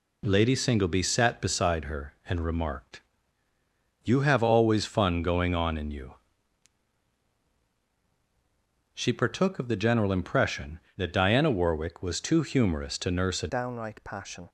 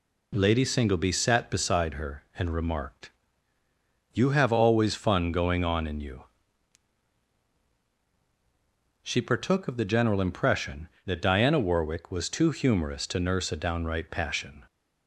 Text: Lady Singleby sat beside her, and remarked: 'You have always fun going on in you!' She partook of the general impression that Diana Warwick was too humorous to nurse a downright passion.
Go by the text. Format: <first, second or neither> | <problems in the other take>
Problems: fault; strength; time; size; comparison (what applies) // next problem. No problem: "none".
second | changes voice at "downright"; from 13.4 s on; 1.0 s long